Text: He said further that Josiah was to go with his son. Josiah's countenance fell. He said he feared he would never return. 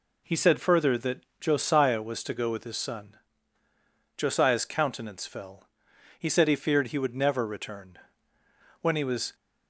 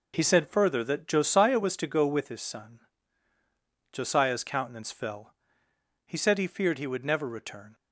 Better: second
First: pauses between "that" and "Josiah"; slight; at 1.2 s; 0.18 s long // goes on to say "When he was"; from 8.8 s on; 0.54 s long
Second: none

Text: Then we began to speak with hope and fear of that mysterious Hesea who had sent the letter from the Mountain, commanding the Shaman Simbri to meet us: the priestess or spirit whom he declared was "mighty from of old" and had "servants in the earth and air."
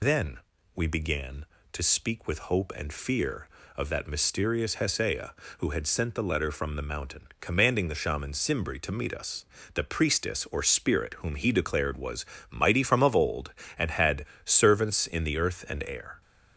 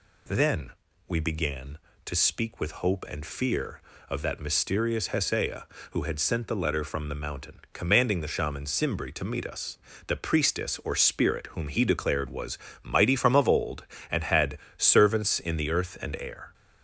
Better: second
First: loses the start of "Then"; at 0.0 s; 85 ms // pauses between "Then" and "we"; slight; at 0.3 s; 0.36 s long // pauses between "was" and "mighty"; slight; at 12.2 s; 0.26 s long // pauses between "had" and "servants"; slight; at 14.2 s; 0.20 s long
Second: pauses between "Then" and "we"; slight; at 0.7 s; 0.36 s long // pauses between "was" and "mighty"; slight; at 12.5 s; 0.26 s long // pauses between "had" and "servants"; slight; at 14.5 s; 0.20 s long

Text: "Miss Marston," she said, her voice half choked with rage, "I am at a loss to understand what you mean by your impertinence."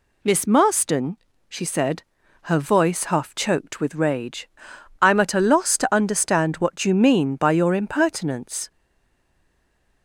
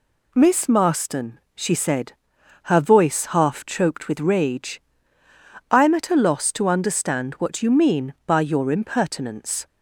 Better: second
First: stays silent after the last word; noticeable; from 8.6 s on; 1.4 s long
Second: none

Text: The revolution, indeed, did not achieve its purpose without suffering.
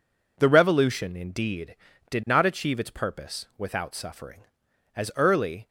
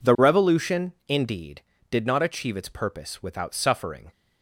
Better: second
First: goes on to say "As early"; noticeable; from 4.9 s on; 0.72 s long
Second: none

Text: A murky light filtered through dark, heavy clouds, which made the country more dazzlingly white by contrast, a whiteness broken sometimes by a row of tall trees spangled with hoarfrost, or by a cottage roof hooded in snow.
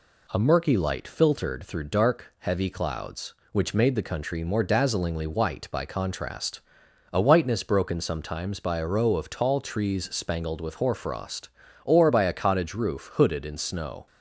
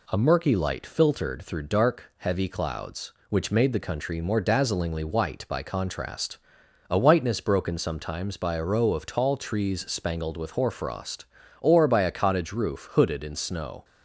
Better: neither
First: none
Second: none

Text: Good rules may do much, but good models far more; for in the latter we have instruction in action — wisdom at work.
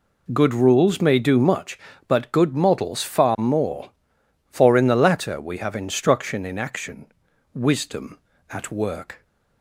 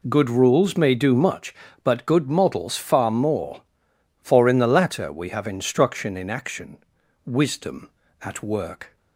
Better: neither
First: none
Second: none

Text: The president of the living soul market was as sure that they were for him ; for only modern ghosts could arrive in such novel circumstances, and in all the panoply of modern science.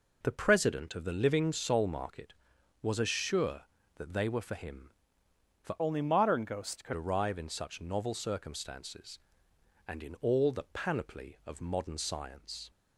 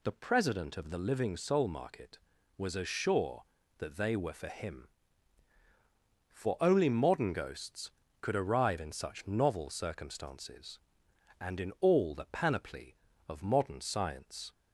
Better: second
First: changes voice from "only" to "could"; from 5.7 to 6.9 s; 1.2 s long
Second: none

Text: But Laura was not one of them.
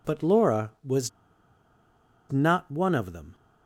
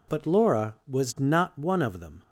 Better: second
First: pauses between "was" and "not"; at 1.0 s; 1.2 s long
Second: none

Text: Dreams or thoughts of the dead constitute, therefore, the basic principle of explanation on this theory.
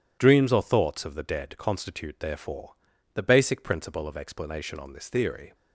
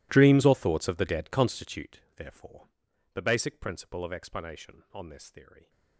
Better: first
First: none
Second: gets quieter; strong; throughout; 22 dB

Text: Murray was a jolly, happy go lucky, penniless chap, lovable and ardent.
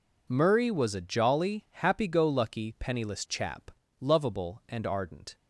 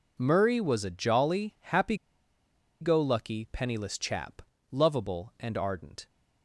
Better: first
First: none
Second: pauses between "happy" and "go"; noticeable; at 1.9 s; 0.86 s long

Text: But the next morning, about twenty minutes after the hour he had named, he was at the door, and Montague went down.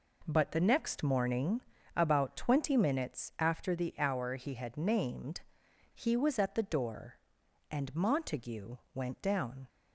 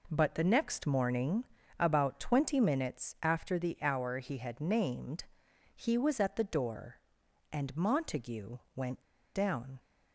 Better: first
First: pauses between "Montague" and "went"; slight; at 8.7 s; 0.18 s long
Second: pauses between "Montague" and "went"; slight; at 8.5 s; 0.18 s long // pauses between "went" and "down"; slight; at 9.0 s; 0.32 s long

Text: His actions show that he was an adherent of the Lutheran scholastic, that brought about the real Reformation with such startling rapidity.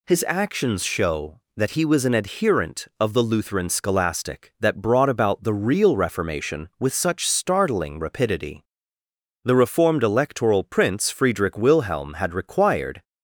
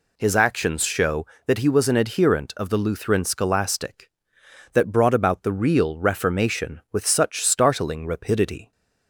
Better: second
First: goes on to say "The reformed Electoral Prince Friedrich Wilhelm had required"; strong; from 9.4 s on; 3.5 s long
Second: none

